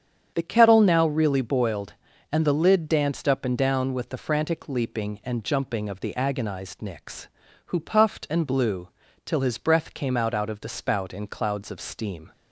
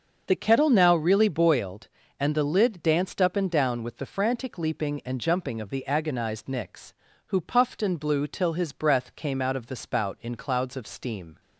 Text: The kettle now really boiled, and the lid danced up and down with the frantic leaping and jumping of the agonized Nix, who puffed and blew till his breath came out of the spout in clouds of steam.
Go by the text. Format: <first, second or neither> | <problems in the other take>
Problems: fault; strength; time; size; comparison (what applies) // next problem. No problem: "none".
second | starts louder than the rest; strong; until 1.3 s; 8 dB; also in the second // pauses between "blew" and "till"; slight; at 8.8 s; 0.36 s long // says "out" twice; at 10.3 s